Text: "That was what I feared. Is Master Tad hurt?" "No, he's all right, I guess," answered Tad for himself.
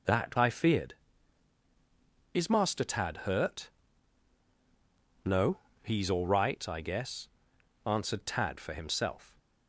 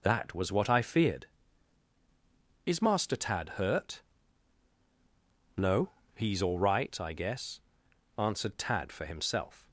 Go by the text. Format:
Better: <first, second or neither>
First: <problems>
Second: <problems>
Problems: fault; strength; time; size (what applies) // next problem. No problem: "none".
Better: second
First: skips "was what"; at 0.3 s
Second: none